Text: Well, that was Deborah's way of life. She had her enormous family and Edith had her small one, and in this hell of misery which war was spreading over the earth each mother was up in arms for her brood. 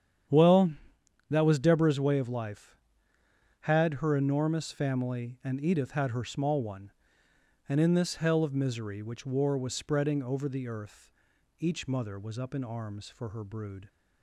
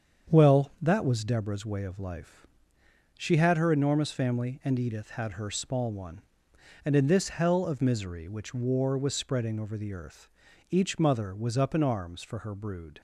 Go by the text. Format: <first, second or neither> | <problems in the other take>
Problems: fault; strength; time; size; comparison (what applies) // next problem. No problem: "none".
second | starts louder than the rest; strong; until 1.8 s; 9 dB; strong in the second // skips "She"; at 3.1 s // pauses between "earth" and "each"; noticeable; at 11.0 s; 0.50 s long; also in the second